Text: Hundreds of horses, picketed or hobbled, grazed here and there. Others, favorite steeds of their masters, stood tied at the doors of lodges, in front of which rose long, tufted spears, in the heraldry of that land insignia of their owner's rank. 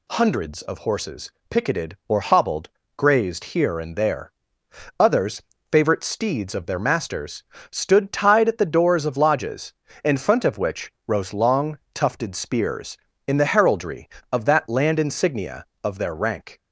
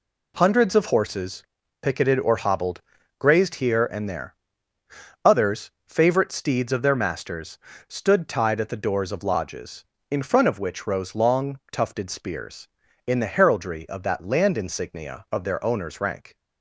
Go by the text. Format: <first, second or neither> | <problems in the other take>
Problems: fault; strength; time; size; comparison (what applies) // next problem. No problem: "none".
second | pauses between "which" and "rose"; slight; at 10.9 s; 0.16 s long // skips "owner's"; at 16.1 s